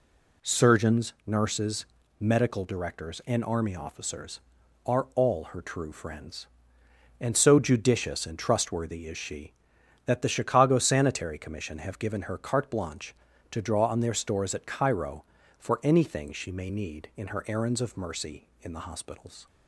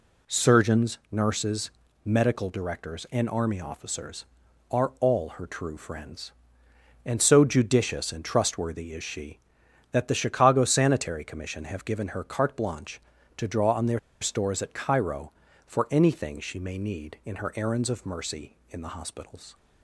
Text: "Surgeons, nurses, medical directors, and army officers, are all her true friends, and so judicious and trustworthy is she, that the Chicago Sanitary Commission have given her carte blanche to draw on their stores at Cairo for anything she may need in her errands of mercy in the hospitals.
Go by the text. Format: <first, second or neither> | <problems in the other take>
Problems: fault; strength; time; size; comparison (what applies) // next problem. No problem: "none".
first | pauses between "their" and "stores"; slight; at 13.9 s; 0.22 s long